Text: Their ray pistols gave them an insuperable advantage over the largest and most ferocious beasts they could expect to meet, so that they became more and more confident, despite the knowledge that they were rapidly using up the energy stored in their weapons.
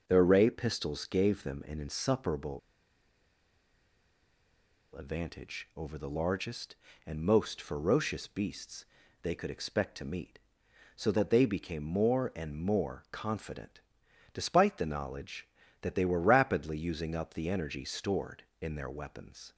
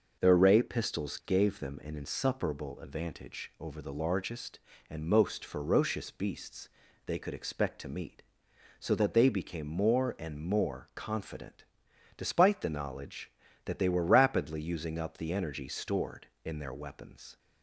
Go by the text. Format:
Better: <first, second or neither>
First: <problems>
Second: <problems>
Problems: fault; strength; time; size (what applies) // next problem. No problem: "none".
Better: second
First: pauses between "insuperable" and "advantage"; strong; at 2.5 s; 2.3 s long // pauses between "beasts" and "they"; at 8.8 s; 0.38 s long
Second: pauses between "beasts" and "they"; at 6.6 s; 0.38 s long